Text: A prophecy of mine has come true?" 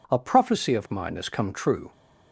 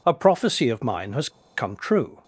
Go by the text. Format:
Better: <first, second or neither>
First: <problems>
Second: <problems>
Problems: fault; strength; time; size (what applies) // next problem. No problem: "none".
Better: first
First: none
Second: pauses between "has" and "come"; slight; at 1.2 s; 0.27 s long